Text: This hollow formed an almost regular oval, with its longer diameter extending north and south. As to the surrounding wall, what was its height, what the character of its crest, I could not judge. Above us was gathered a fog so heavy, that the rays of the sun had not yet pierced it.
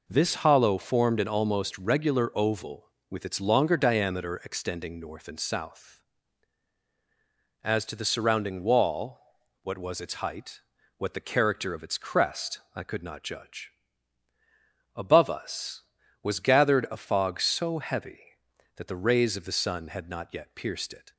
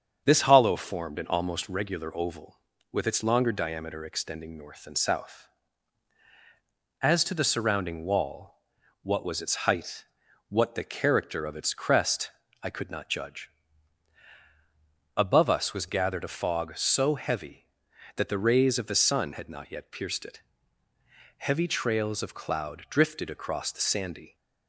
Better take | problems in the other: first | starts louder than the rest; strong; until 1.2 s; 7.5 dB // goes on to say "Heavy trails of cloud drifted across the sandy"; strong; from 21.3 s on; 2.9 s long

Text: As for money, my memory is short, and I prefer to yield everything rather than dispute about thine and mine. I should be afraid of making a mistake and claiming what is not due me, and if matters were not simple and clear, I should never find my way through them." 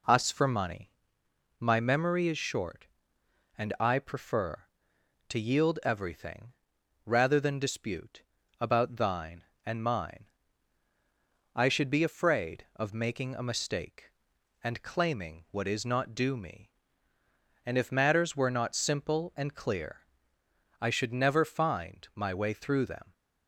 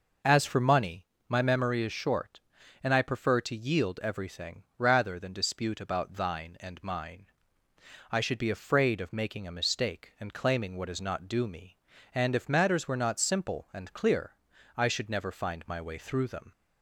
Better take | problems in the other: second | says "Us" for "As"; at 0.0 s // pauses between "everything" and "rather"; noticeable; at 6.4 s; 0.58 s long // pauses between "dispute" and "about"; at 8.2 s; 0.40 s long

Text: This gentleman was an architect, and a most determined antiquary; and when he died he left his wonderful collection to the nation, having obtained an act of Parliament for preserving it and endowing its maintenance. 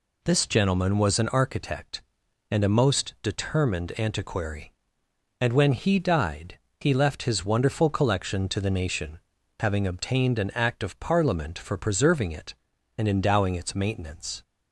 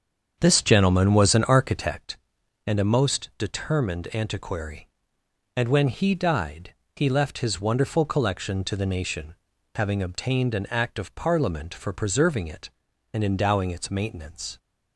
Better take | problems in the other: first | starts louder than the rest; strong; until 2.1 s; 7 dB // pauses between "died" and "he"; slight; at 6.7 s; 0.20 s long; slight in the first

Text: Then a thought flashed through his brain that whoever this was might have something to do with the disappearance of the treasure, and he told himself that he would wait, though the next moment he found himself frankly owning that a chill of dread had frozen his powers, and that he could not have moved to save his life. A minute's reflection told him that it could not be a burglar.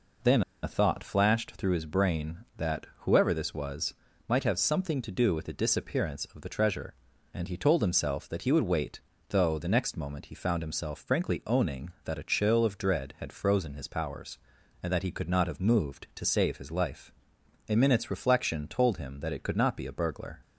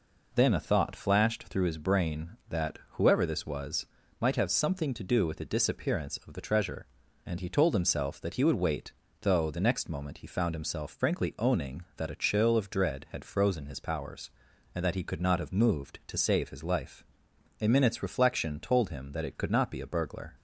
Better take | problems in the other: second | pauses between "Then" and "a"; slight; at 0.4 s; 0.20 s long // pauses between "was" and "might"; slight; at 3.9 s; 0.34 s long; slight in the second

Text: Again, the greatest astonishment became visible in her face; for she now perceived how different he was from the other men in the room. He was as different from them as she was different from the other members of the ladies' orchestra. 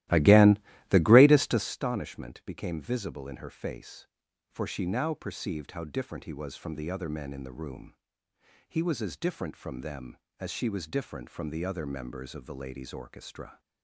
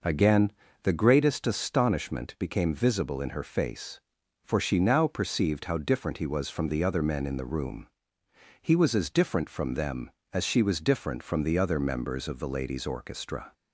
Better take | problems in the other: second | starts louder than the rest; strong; until 1.8 s; 16 dB

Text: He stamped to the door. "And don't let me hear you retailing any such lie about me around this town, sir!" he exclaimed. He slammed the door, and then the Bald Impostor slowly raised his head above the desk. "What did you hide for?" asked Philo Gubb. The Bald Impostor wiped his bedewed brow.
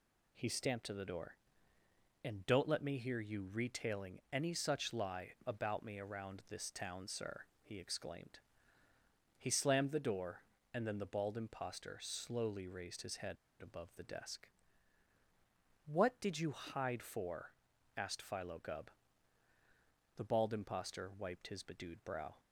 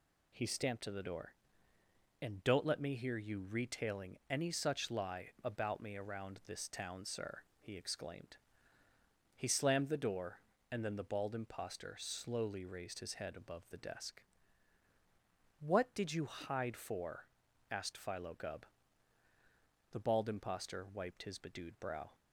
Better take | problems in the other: second | pauses between "head" and "above"; slight; at 13.3 s; 0.25 s long

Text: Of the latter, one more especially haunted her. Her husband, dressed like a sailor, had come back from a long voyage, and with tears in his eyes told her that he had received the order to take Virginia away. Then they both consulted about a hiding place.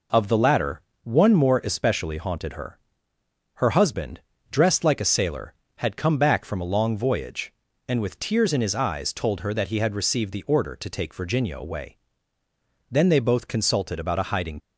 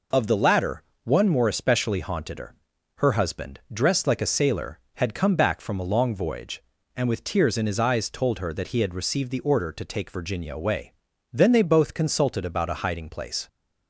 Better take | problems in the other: second | stops before "place"; at 14.5 s

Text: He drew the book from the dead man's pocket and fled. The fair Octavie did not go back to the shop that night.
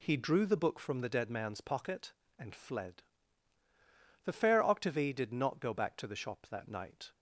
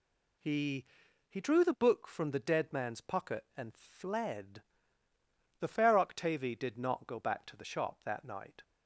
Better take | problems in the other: first | says "He" twice; at 1.2 s

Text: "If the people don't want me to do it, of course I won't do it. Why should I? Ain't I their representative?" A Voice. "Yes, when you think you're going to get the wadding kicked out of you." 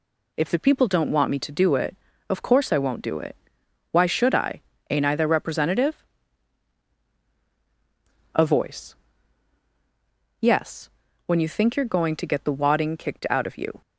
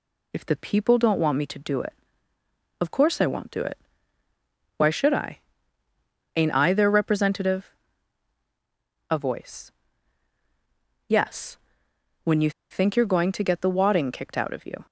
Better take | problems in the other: first | pauses between "you" and "think"; slight; at 12.4 s; 0.20 s long

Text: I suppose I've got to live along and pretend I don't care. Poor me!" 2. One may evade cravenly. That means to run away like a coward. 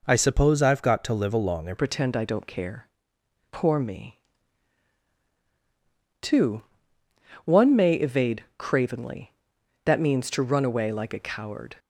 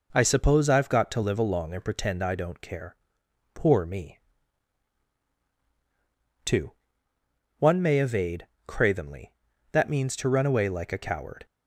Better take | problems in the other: second | changes voice at "pretend"; from 1.7 s on; 10.0 s long // pauses between "evade" and "cravenly"; slight; at 8.4 s; 0.16 s long; slight in the second

